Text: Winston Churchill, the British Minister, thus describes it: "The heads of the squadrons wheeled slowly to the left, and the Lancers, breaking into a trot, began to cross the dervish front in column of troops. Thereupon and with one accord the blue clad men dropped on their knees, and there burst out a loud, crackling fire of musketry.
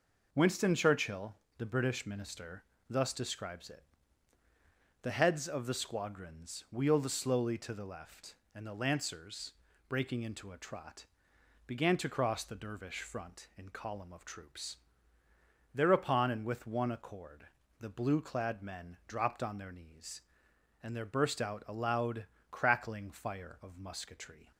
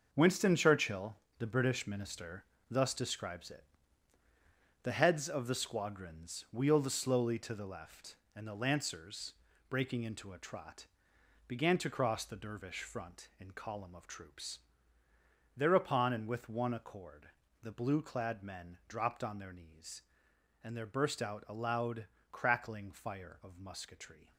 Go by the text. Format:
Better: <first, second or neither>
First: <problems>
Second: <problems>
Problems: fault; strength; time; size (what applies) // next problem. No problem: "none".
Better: first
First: pauses between "accord" and "the"; slight; at 17.4 s; 0.32 s long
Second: gets quieter; strong; throughout; 9 dB // pauses between "accord" and "the"; slight; at 17.2 s; 0.32 s long